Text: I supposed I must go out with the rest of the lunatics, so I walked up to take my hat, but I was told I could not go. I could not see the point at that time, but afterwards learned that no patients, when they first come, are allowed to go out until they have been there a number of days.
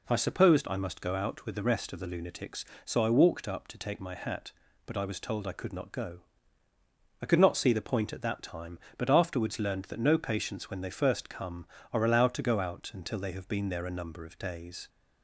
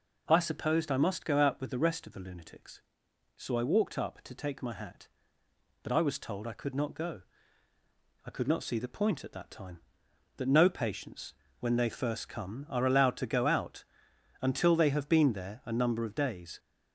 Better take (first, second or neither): first